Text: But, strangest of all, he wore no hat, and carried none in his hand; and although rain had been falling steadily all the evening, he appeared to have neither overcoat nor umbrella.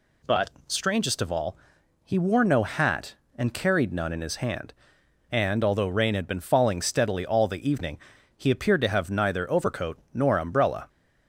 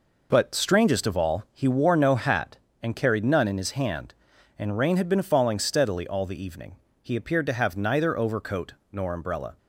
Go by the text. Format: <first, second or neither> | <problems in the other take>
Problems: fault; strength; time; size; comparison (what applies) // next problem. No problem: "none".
first | skips "although"; at 4.7 s // pauses between "overcoat" and "nor"; slight; at 8.7 s; 0.22 s long; slight in the first